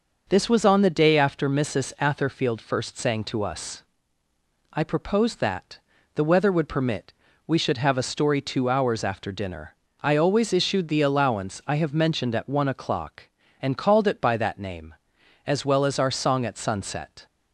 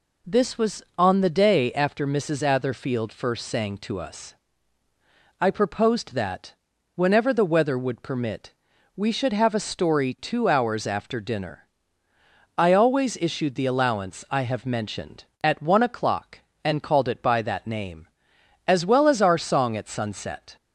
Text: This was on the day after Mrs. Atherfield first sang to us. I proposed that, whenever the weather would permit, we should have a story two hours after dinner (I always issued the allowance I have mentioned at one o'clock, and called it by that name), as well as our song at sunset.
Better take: second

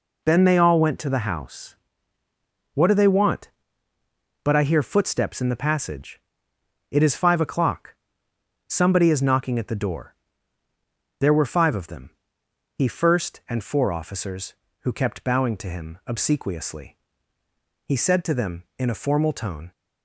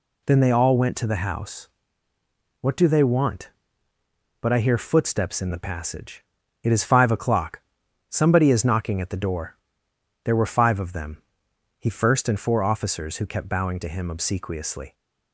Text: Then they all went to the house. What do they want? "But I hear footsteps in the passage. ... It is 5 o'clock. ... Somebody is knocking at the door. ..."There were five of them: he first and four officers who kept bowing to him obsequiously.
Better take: second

